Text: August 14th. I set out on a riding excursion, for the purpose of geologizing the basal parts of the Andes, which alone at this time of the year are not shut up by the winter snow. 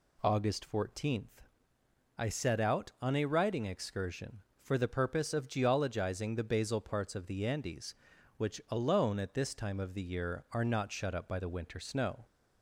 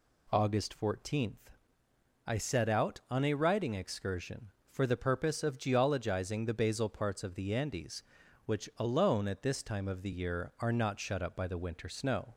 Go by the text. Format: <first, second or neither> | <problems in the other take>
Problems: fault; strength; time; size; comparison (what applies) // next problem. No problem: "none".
neither | none